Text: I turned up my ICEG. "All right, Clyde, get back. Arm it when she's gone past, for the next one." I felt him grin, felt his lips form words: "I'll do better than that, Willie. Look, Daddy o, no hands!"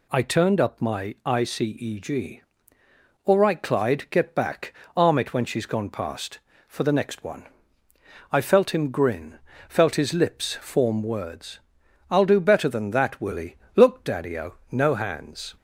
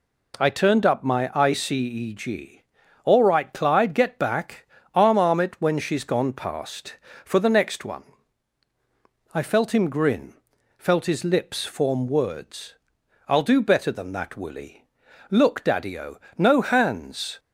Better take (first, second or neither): first